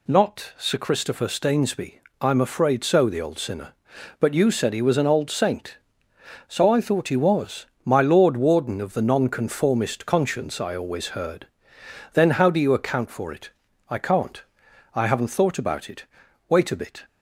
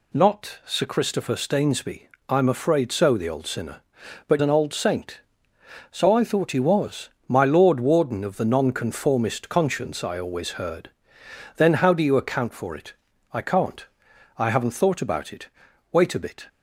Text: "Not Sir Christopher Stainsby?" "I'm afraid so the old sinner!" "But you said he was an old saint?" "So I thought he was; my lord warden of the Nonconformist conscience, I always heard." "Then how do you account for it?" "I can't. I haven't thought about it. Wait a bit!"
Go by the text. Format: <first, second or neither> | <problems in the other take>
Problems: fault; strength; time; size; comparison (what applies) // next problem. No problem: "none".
first | skips "you said he was"; at 4.4 s